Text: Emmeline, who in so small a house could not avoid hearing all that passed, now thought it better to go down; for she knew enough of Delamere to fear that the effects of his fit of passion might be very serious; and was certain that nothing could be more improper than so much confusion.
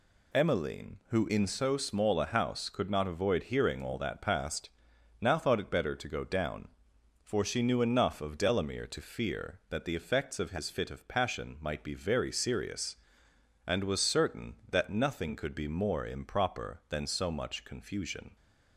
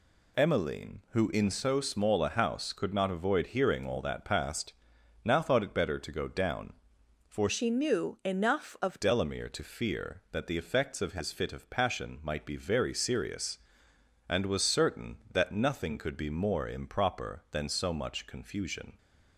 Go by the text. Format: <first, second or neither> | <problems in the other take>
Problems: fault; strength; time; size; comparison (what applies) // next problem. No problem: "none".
first | changes voice from "she" to "of"; from 7.4 to 9.0 s; 1.6 s long